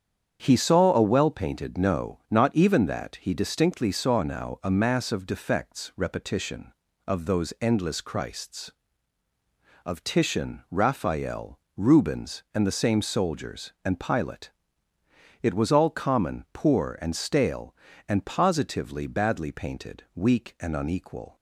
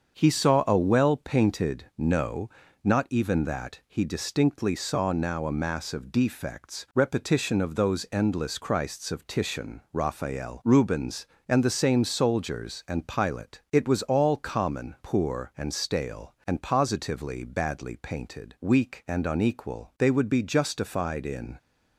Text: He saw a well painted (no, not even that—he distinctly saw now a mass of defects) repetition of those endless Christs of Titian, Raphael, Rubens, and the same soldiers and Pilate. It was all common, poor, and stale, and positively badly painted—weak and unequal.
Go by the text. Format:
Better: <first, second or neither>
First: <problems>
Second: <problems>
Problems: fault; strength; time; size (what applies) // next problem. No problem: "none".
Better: first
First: starts louder than the rest; strong; until 1.4 s; 7.5 dB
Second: starts louder than the rest; until 1.2 s; 6.5 dB // goes on to say "They would be justified in"; from 19.9 s on; 1.6 s long